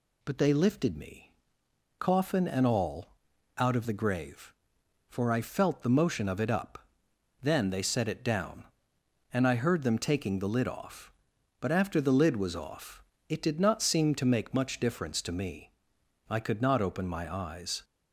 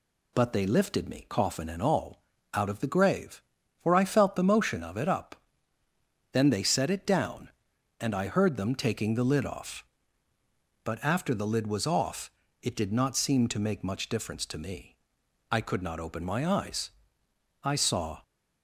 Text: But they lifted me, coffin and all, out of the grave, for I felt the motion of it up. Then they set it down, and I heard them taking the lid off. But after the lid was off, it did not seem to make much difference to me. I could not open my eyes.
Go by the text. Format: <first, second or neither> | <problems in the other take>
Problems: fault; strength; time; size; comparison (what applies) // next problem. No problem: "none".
first | goes on to say "I saw"; from 17.6 s on; 0.60 s long